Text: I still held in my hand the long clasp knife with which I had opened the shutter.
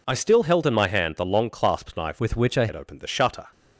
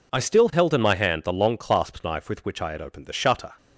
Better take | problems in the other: second | changes voice from "with" to "I"; from 2.1 to 2.6 s; 0.5 s long

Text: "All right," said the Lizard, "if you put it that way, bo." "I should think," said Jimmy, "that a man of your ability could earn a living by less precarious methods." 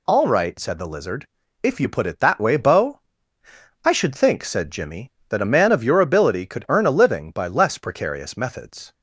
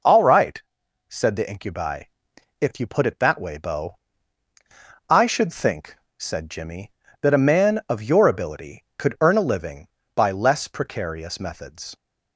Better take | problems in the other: first | says "Incubi" for "Lizard"; at 1.4 s

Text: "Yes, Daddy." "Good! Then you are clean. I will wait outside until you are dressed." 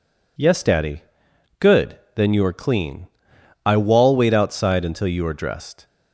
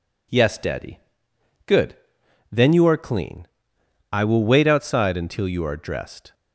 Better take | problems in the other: second | says "wall" for "will"; at 3.7 s

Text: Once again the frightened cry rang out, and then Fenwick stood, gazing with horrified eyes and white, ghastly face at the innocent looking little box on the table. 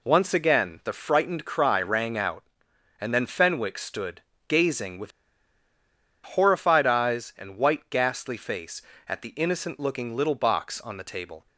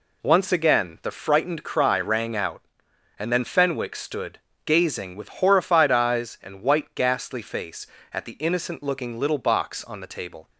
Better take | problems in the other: second | pauses between "with" and "horrified"; at 5.1 s; 1.1 s long

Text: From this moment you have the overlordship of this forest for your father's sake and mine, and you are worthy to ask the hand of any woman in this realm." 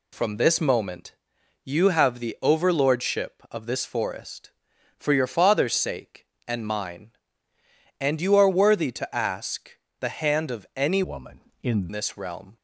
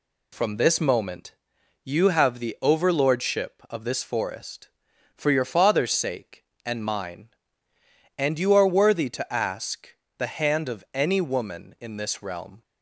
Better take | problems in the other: second | pauses between "moment" and "you"; noticeable; at 1.1 s; 0.48 s long; noticeable in the second // pauses between "ask" and "the"; slight; at 9.7 s; 0.28 s long; slight in the second // changes voice from "woman" to "in"; from 11.0 to 11.8 s; 0.8 s long

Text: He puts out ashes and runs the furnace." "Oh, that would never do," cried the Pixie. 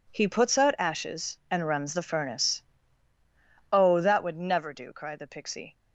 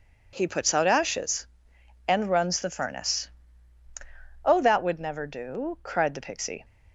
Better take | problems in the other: neither | none

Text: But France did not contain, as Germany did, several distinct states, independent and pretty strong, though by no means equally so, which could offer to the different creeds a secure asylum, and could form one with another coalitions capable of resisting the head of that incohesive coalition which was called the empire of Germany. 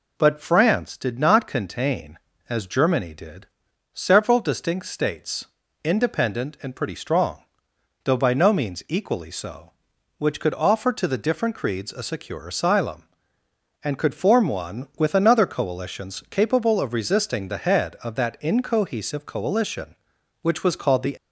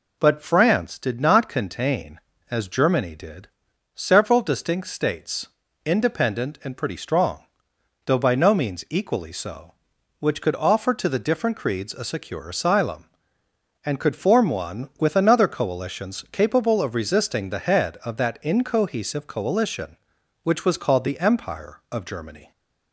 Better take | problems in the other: second | stops before "empire of Germany"; at 21.1 s

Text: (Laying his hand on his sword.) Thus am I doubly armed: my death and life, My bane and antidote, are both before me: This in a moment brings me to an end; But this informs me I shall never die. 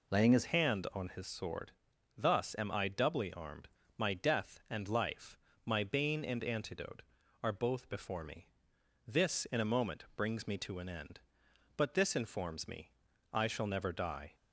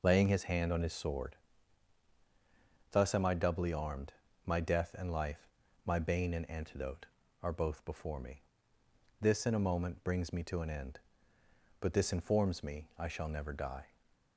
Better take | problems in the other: second | changes voice at "hand"; from 0.4 s on; 13.9 s long // pauses between "me" and "I"; at 12.9 s; 0.42 s long

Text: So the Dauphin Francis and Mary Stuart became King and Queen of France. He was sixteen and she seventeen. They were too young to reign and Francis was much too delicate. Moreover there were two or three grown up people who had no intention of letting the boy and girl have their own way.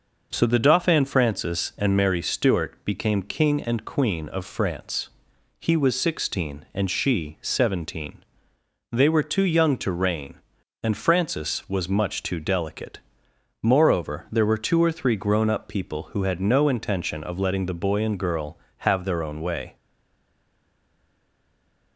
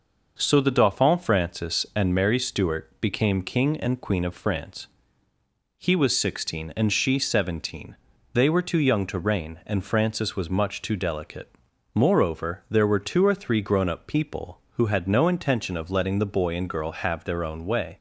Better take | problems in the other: second | stays silent after the last word; from 19.7 s on; 2.2 s long

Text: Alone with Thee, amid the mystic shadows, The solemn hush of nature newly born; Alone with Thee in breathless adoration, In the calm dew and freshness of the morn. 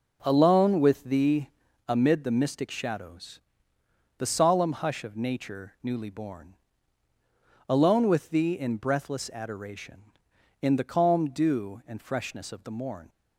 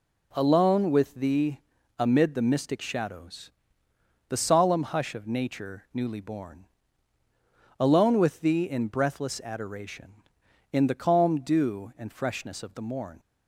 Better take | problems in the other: second | starts louder than the rest; noticeable; until 1.9 s; 5 dB

